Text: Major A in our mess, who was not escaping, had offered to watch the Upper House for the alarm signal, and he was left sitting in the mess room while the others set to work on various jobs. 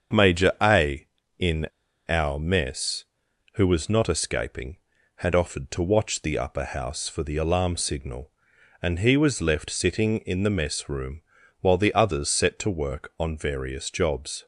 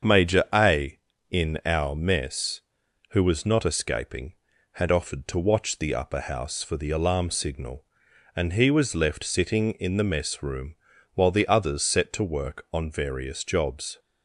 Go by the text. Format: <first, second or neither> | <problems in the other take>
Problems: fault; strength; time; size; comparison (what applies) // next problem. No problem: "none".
second | starts louder than the rest; until 1.5 s; 7 dB; also in the second // pauses between "in" and "our"; at 1.6 s; 0.39 s long // pauses between "room" and "while"; at 11.2 s; 0.38 s long; also in the second